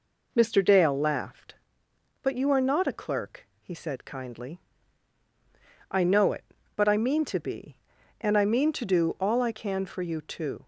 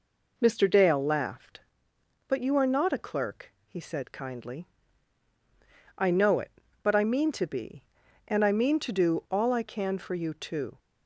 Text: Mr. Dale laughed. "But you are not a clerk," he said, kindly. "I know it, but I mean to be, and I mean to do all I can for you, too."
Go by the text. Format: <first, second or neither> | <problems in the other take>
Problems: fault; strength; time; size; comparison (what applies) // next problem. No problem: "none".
neither | none